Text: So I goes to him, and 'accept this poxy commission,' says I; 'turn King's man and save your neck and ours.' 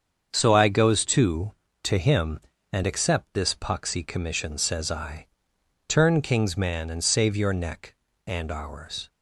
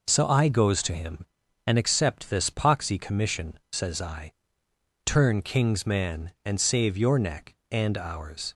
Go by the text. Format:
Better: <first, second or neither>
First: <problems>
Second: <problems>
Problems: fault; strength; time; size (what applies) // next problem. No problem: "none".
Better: second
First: starts louder than the rest; until 1.3 s; 7 dB // says "to" twice; at 1.8 s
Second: none